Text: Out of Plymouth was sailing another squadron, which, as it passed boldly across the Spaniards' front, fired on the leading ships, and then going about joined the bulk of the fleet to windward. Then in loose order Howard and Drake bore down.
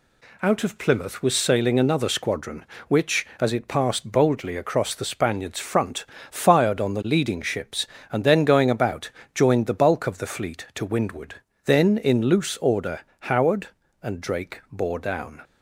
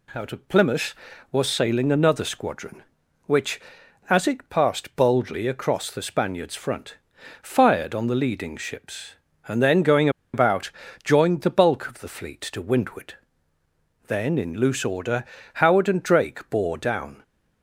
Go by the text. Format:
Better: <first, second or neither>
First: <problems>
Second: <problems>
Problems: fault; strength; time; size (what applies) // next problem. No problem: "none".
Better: first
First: pauses between "about" and "joined"; slight; at 9.0 s; 0.24 s long // pauses between "order" and "Howard"; slight; at 13.0 s; 0.18 s long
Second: pauses between "going" and "about"; slight; at 10.0 s; 0.24 s long // pauses between "about" and "joined"; slight; at 10.7 s; 0.32 s long // pauses between "order" and "Howard"; slight; at 15.2 s; 0.30 s long